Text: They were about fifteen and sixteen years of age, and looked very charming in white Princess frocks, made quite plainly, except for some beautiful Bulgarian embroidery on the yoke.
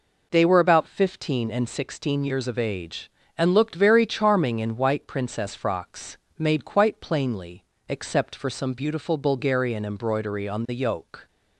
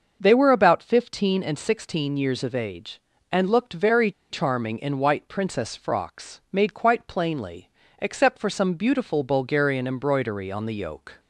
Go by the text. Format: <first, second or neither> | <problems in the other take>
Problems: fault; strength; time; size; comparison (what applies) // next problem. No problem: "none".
first | starts louder than the rest; until 1.2 s; 6.5 dB // pauses between "very" and "charming"; slight; at 4.1 s; 0.19 s long